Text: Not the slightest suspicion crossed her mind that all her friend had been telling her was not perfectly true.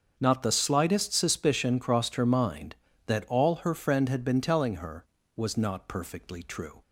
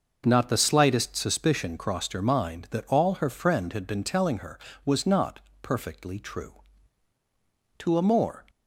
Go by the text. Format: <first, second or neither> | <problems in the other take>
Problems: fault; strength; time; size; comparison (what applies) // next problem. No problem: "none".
first | starts louder than the rest; noticeable; until 1.2 s; 6 dB; also in the first // pauses between "not" and "perfectly"; slight; at 5.3 s; 0.22 s long // goes on to say "To a more"; noticeable; from 7.8 s on; 0.64 s long